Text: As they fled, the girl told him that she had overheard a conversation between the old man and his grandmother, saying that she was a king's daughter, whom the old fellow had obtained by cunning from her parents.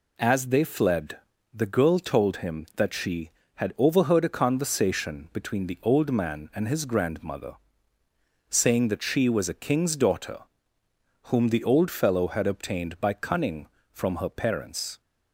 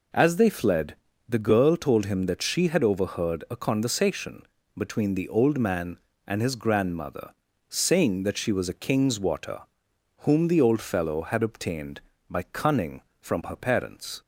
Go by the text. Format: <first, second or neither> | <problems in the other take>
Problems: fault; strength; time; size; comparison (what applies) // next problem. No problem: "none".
first | pauses between "conversation" and "between"; slight; at 4.4 s; 0.34 s long // says "water" for "daughter"; at 9.1 s